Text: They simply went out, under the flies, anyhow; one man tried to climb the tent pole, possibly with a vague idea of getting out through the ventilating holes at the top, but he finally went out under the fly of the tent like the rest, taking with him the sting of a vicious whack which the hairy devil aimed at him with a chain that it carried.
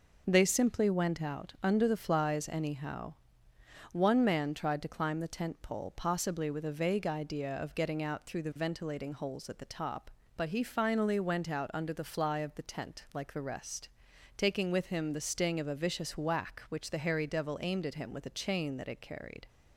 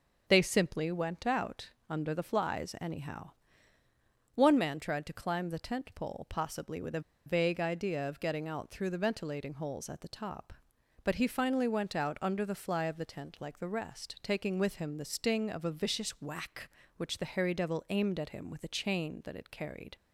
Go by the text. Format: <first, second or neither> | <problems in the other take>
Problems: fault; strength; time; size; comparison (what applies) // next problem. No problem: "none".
first | starts louder than the rest; until 1.2 s; 6 dB // pauses between "a" and "vague"; slight; at 6.9 s; 0.26 s long